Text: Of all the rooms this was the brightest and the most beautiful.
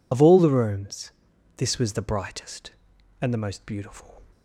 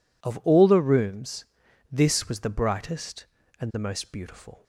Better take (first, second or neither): second